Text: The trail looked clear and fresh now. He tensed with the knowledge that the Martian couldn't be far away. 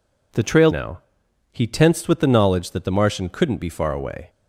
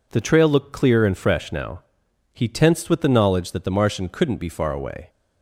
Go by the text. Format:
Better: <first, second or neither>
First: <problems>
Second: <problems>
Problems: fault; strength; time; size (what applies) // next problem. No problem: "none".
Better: second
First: skips "looked clear and fresh"; at 0.6 s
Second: none